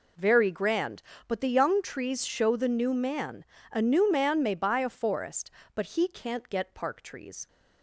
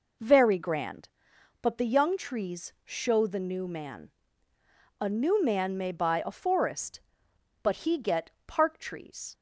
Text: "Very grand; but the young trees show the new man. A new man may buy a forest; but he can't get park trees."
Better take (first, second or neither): first